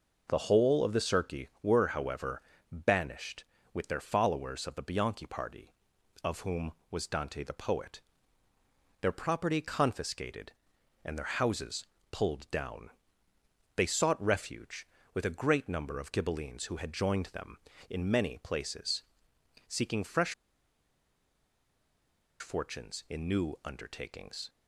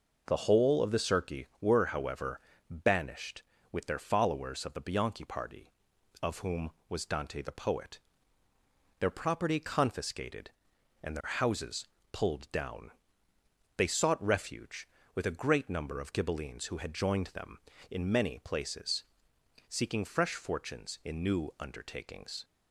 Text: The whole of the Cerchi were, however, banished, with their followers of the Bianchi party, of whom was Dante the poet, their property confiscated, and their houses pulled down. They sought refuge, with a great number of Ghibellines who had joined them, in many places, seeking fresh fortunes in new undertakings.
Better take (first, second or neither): second